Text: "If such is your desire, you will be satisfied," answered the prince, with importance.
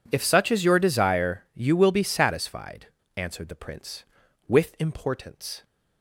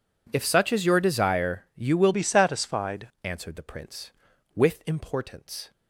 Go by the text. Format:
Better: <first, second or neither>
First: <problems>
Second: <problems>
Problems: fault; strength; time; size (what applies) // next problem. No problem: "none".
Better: first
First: none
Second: changes voice from "be" to "satisfied"; from 2.1 to 3.0 s; 0.9 s long